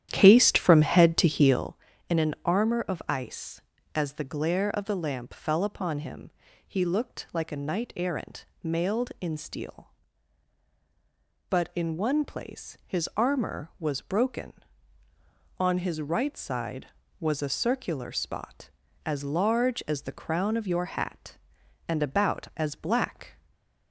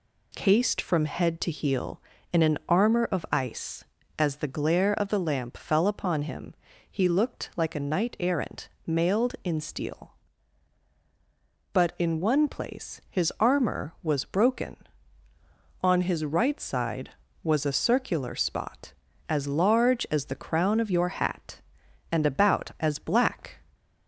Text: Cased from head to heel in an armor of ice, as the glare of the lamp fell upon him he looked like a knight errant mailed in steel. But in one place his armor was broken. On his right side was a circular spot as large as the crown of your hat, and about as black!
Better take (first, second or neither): second